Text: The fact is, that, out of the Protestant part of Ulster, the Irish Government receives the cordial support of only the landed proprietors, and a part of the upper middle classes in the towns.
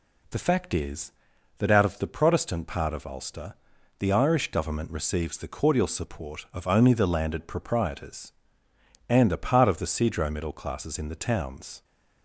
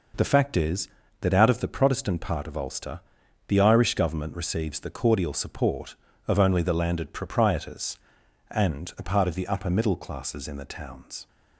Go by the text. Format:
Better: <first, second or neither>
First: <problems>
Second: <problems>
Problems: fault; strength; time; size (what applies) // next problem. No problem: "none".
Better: second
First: says "cedro" for "upper"; at 9.8 s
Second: none